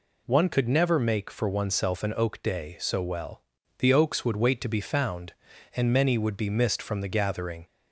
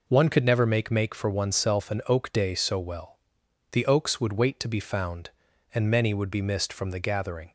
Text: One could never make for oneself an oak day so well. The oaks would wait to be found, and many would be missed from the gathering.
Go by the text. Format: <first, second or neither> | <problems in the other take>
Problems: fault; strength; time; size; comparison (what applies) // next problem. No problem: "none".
first | says "make" twice; at 0.8 s